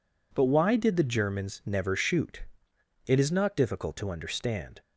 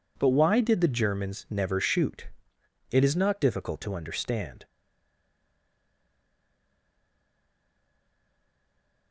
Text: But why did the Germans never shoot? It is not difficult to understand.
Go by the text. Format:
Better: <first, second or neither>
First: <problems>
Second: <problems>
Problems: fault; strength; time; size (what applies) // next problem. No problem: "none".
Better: first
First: none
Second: stays silent after the last word; strong; from 4.6 s on; 4.5 s long